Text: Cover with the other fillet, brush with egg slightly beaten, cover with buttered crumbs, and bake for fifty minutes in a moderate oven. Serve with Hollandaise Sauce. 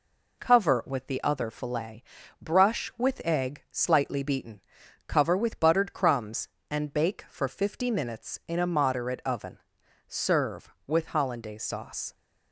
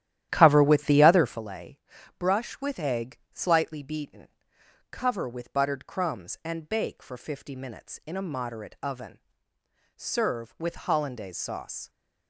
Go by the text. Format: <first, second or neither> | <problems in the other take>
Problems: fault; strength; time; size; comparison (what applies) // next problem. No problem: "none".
first | starts louder than the rest; strong; until 1.4 s; 12 dB